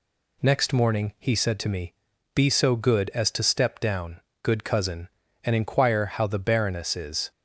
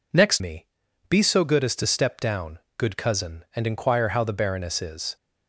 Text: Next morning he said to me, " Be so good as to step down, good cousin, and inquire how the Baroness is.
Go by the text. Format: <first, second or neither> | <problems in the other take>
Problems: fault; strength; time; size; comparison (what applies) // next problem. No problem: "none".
first | skips "morning he said to"; at 0.4 s